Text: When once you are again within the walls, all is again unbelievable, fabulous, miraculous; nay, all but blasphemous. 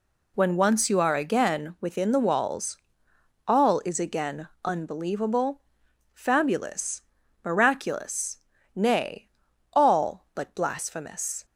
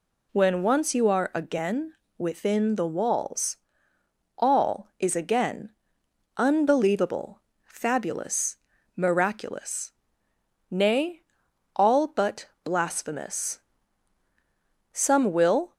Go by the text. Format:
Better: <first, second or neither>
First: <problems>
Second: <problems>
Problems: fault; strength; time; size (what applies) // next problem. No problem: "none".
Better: first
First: pauses between "again" and "unbelievable"; slight; at 4.4 s; 0.16 s long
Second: pauses between "again" and "within"; slight; at 1.9 s; 0.24 s long // pauses between "again" and "unbelievable"; noticeable; at 5.7 s; 0.66 s long // pauses between "but" and "blasphemous"; slight; at 12.4 s; 0.18 s long // goes on to say "Some will"; noticeable; from 14.9 s on; 0.80 s long